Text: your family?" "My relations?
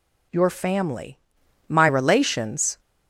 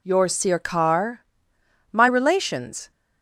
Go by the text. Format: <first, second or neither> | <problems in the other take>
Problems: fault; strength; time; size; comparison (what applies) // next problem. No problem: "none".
first | says "sirkar" for "family"; at 0.2 s